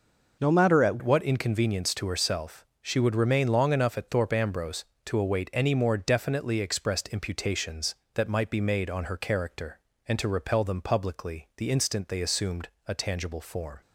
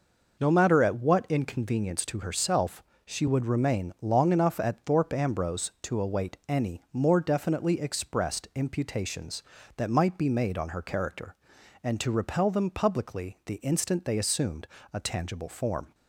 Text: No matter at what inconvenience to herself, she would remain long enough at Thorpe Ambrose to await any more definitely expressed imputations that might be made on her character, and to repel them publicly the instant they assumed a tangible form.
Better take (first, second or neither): second